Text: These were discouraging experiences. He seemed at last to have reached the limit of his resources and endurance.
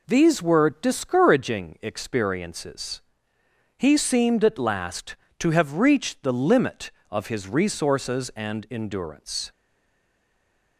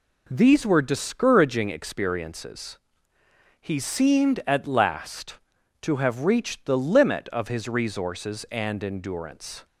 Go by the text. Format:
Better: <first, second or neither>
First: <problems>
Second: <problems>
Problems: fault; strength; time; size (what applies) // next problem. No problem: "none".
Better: second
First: stays silent after the last word; noticeable; from 9.5 s on; 1.2 s long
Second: none